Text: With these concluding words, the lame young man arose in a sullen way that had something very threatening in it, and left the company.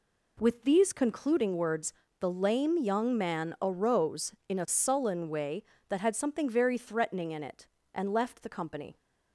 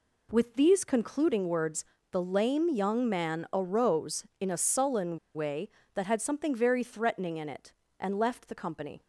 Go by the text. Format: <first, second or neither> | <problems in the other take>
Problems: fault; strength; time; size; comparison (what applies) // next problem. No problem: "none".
first | pauses between "sullen" and "way"; slight; at 5.1 s; 0.16 s long